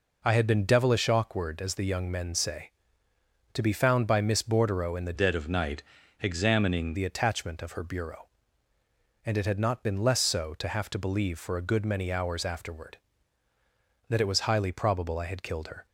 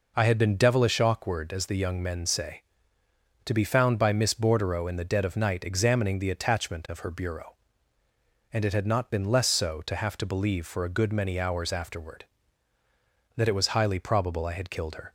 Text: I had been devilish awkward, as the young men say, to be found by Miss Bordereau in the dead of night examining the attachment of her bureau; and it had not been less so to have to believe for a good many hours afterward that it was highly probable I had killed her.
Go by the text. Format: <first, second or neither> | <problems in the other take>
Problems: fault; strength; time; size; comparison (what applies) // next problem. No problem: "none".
second | changes voice from "dead" to "examining"; from 5.1 to 6.9 s; 1.8 s long // pauses between "night" and "examining"; at 5.8 s; 0.38 s long